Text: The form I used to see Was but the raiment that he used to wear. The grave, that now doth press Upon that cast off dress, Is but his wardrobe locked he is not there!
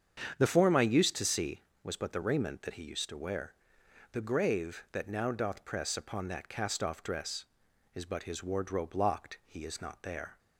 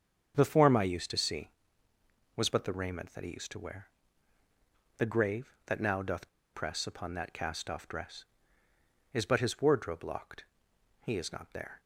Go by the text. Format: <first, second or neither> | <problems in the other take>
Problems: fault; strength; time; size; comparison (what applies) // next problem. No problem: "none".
first | starts louder than the rest; strong; until 1.3 s; 7.5 dB; strong in the first // pauses between "doth" and "press"; slight; at 6.2 s; 0.24 s long // pauses between "locked" and "he"; noticeable; at 10.4 s; 0.58 s long